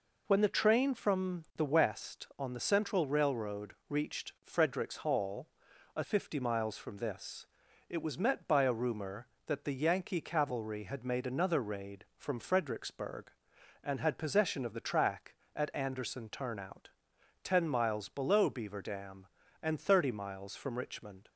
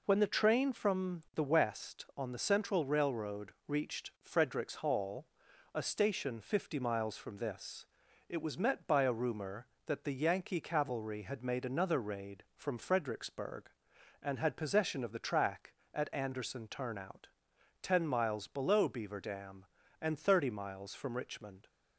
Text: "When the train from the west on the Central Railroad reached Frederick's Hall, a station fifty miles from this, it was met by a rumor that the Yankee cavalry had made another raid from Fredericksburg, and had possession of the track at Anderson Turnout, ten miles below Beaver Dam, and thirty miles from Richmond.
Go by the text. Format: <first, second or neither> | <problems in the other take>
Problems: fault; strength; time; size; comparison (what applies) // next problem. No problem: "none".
second | pauses between "Railroad" and "reached"; slight; at 3.7 s; 0.16 s long; slight in the second // skips "station"; at 6.0 s